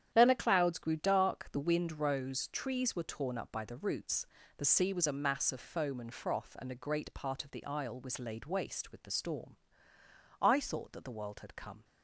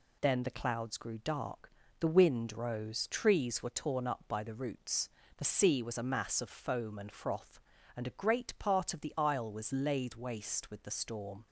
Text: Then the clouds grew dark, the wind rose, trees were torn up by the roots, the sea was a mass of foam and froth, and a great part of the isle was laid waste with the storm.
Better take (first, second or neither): second